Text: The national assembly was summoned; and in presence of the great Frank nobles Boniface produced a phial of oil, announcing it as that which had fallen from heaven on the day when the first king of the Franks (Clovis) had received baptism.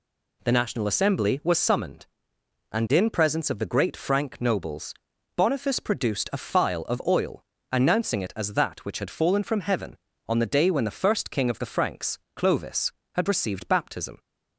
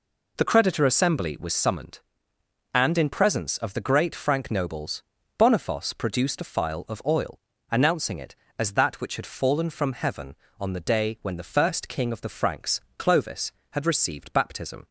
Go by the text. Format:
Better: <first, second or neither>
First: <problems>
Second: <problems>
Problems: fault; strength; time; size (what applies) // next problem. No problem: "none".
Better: first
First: pauses between "nobles" and "Boniface"; at 4.9 s; 0.42 s long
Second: says "creditor" for "national"; at 0.4 s // pauses between "nobles" and "Boniface"; slight; at 5.0 s; 0.36 s long